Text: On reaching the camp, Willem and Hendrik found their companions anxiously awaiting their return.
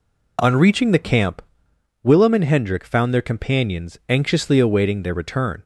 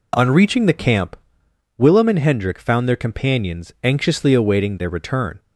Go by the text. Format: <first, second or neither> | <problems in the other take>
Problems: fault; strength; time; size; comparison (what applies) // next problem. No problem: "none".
neither | none